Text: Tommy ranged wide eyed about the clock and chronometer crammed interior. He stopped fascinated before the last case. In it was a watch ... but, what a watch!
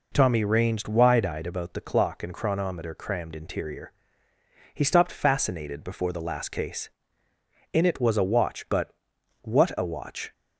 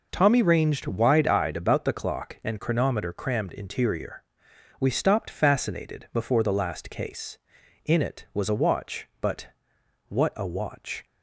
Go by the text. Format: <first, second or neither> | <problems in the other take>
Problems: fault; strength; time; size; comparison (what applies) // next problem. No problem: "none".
first | says "We" for "He"; at 4.7 s